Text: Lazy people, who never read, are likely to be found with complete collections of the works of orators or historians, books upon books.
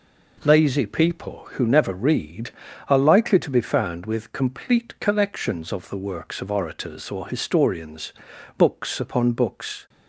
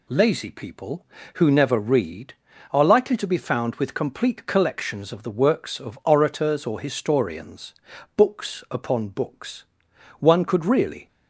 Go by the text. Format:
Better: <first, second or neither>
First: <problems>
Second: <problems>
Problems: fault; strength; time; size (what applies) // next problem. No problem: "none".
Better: first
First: none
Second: goes on to say "One could really"; noticeable; from 10.1 s on; 0.88 s long